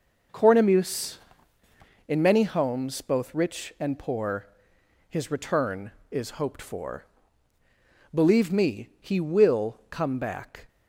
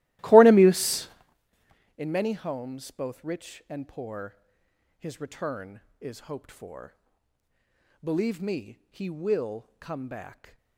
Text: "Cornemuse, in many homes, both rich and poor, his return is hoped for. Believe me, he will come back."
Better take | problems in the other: first | starts louder than the rest; strong; until 1.3 s; 17 dB

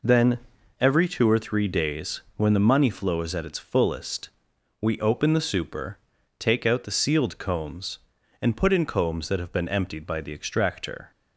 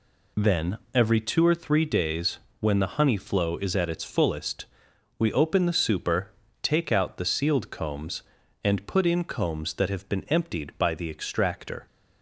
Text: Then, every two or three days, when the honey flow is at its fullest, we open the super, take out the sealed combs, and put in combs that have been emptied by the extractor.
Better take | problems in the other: second | says "money" for "honey"; at 2.5 s

